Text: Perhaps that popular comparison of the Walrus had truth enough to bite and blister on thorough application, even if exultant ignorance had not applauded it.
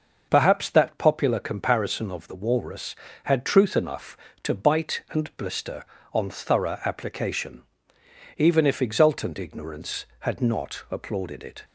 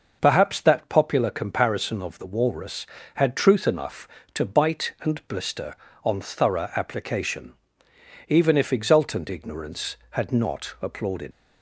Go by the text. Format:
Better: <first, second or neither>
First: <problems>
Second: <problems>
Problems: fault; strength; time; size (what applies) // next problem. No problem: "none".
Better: first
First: starts louder than the rest; noticeable; until 1.3 s; 6 dB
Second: starts louder than the rest; noticeable; until 1.2 s; 6 dB // stops before "it"; at 11.3 s